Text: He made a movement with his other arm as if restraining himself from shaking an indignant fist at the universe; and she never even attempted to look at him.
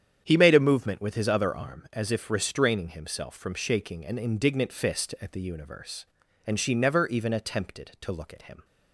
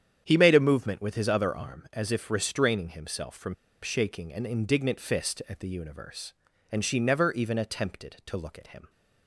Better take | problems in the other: first | starts louder than the rest; strong; until 1.2 s; 8.5 dB; strong in the first // pauses between "from" and "shaking"; slight; at 3.5 s; 0.29 s long

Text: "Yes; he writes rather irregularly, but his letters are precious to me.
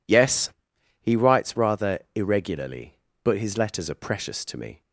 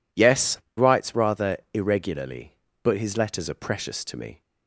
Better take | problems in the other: first | skips "he"; at 0.6 s // pauses between "rather" and "irregularly"; slight; at 1.5 s; 0.16 s long; slight in the first

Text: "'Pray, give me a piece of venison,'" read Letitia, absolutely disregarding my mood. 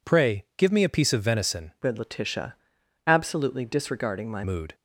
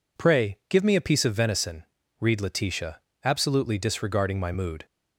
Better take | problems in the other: second | changes voice from "read" to "my"; from 1.8 to 4.4 s; 2.6 s long

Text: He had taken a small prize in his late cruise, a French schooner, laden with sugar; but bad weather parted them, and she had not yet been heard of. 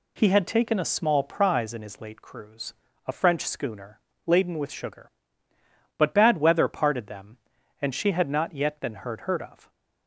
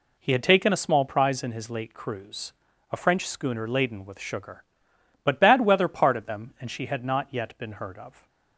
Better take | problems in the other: second | says "heard" twice; at 9.2 s

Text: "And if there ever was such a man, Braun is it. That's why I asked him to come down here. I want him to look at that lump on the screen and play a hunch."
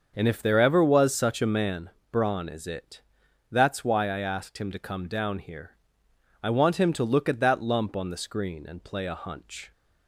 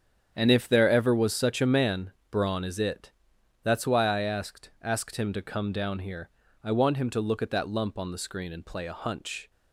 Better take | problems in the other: first | starts louder than the rest; strong; until 1.3 s; 8 dB; also in the first // says "asked" twice; at 4.8 s

